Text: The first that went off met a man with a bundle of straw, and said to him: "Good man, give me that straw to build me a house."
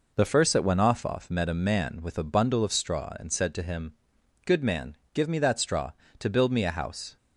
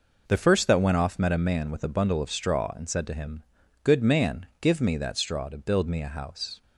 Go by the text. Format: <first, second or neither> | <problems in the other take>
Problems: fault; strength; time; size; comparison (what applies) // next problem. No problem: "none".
second | says "off" twice; at 1.0 s